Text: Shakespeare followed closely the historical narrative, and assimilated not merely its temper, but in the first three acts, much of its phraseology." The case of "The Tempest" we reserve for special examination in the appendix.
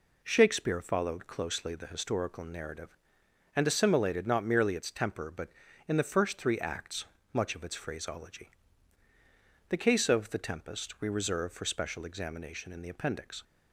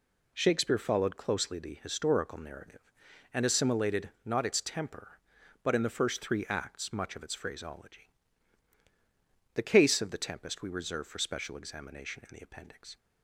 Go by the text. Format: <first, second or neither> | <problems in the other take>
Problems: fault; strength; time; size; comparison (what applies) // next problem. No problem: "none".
first | skips "merely"; at 4.4 s